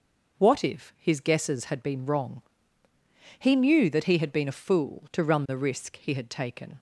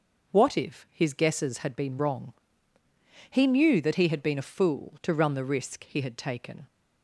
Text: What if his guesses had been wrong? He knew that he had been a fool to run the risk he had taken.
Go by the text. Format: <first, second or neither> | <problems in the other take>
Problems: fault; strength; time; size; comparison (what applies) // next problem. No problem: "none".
neither | none